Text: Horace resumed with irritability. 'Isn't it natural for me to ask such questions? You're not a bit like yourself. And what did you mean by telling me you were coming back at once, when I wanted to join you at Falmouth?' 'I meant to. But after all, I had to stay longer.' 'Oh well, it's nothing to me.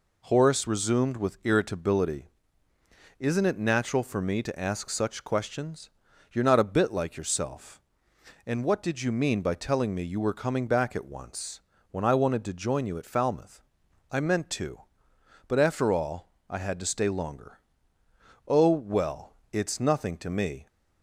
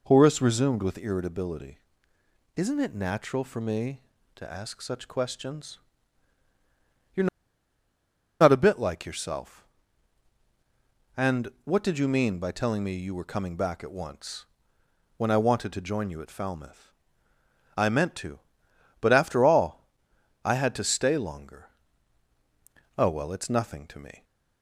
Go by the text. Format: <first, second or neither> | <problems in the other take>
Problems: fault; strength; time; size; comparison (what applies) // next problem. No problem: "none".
first | pauses between "You're" and "not"; at 7.2 s; 1.1 s long